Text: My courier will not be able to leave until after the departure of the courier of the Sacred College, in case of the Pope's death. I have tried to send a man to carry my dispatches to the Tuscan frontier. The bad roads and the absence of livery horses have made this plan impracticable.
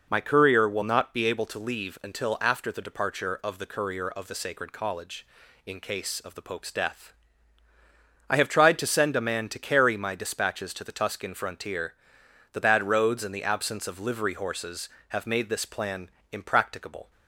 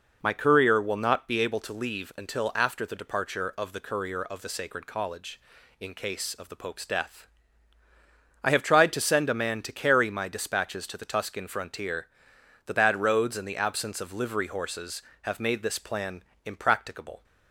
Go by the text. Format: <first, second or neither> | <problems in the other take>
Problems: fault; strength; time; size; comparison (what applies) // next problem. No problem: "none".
neither | pauses between "plan" and "impracticable"; slight; the same in both